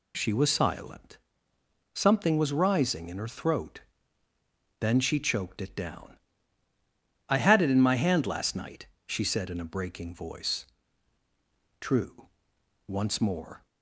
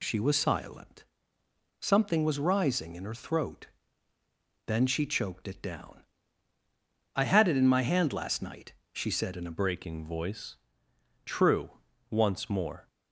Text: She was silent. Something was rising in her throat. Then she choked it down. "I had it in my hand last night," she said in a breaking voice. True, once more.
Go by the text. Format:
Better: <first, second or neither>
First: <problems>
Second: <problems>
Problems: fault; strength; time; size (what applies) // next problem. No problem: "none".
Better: first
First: none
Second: changes voice at "breaking"; from 9.5 s on; 3.3 s long